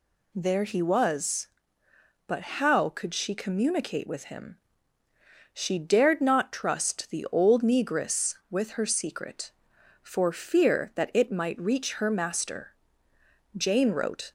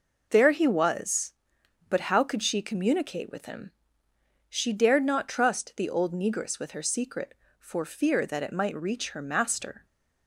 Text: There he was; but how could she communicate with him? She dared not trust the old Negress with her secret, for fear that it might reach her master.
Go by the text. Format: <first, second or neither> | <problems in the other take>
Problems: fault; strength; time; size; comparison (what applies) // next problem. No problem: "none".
second | goes on to say "Jane wrote"; noticeable; from 13.5 s on; 0.76 s long